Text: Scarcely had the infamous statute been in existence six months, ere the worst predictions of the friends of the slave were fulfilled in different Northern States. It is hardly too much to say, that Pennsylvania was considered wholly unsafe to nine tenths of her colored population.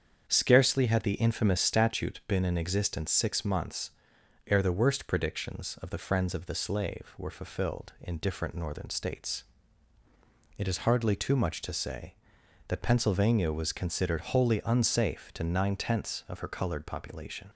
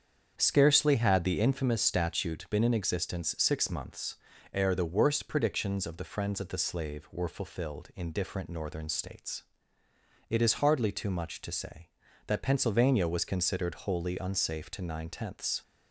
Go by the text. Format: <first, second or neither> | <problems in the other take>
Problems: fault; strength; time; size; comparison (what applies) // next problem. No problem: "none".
first | starts louder than the rest; strong; until 1.3 s; 7.5 dB; strong in the first // stops before "of her colored population"; at 15.6 s